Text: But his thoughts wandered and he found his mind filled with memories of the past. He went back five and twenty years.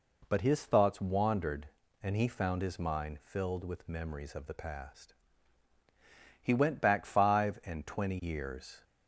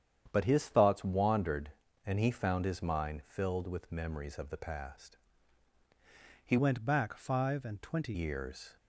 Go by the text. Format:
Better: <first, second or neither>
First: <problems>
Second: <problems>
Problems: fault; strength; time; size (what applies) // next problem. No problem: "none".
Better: first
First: none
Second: starts louder than the rest; strong; until 1.3 s; 9 dB // changes voice from "went" to "twenty"; from 6.5 to 8.1 s; 1.6 s long